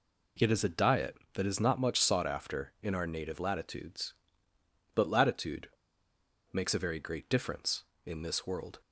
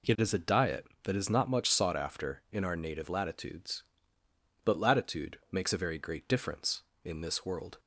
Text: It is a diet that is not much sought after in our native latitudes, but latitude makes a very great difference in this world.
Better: second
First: pauses between "latitude" and "makes"; noticeable; at 5.6 s; 0.84 s long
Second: none

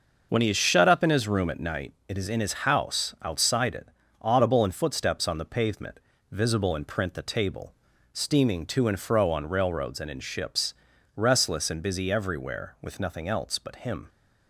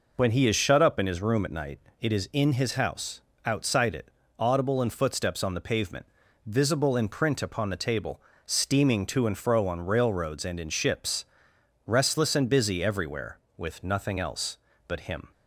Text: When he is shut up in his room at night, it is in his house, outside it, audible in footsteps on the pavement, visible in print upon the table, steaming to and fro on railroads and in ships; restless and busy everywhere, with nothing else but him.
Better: second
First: skips "upon"; at 7.1 s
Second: none

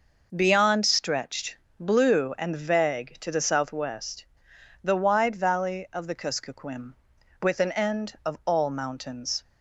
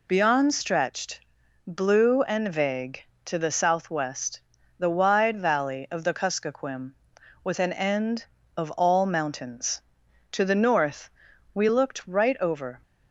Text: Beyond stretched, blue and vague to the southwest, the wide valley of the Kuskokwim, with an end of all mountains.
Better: first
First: none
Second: goes on to say "To the north we looked right over"; strong; from 10.3 s on; 2.4 s long

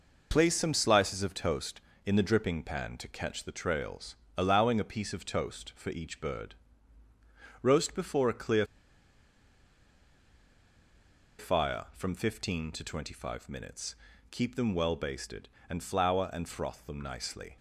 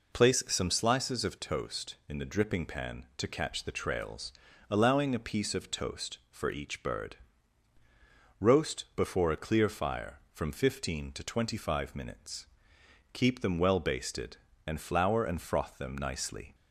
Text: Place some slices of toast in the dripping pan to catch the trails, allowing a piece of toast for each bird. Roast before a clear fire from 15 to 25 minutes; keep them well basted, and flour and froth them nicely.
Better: second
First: pauses between "clear" and "fire"; strong; at 8.6 s; 2.7 s long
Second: none

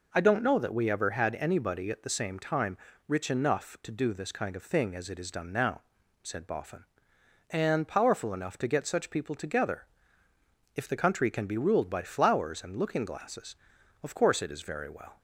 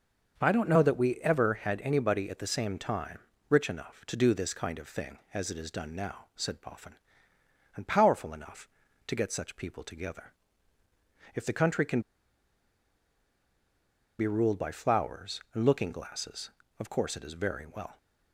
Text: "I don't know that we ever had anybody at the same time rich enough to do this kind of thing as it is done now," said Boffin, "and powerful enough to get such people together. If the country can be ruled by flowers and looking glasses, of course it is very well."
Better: first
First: pauses between "time" and "rich"; slight; at 2.7 s; 0.30 s long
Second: starts louder than the rest; until 1.4 s; 6.5 dB // pauses between "time" and "rich"; slight; at 3.2 s; 0.28 s long // pauses between "can" and "be"; strong; at 12.0 s; 2.1 s long

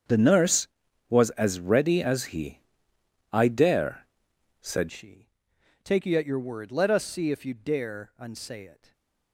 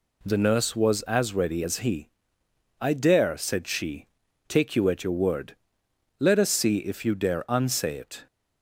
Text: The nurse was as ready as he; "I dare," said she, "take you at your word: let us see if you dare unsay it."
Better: second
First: starts louder than the rest; strong; until 1.5 s; 7.5 dB // changes voice at "she"; from 4.9 s on; 4.0 s long // stays silent after the last word; slight; from 8.7 s on; 0.6 s long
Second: none

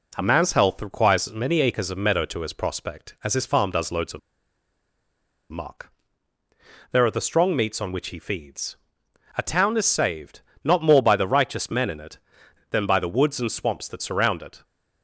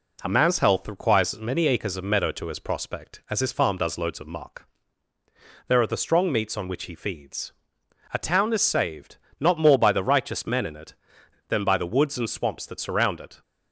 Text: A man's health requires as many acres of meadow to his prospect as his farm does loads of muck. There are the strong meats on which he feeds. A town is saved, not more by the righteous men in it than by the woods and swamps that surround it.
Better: second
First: pauses between "of" and "muck"; strong; at 4.1 s; 1.3 s long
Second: none

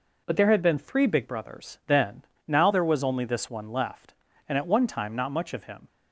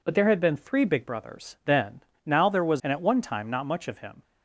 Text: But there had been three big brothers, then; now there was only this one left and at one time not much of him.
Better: first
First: none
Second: skips "only this one left"; at 2.8 s

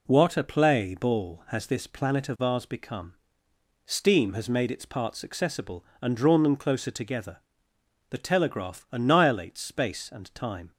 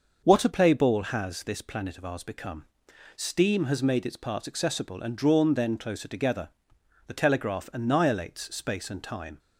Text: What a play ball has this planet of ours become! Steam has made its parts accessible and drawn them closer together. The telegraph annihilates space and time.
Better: first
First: none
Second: starts louder than the rest; until 1.2 s; 6 dB // says "then" for "them"; at 5.5 s

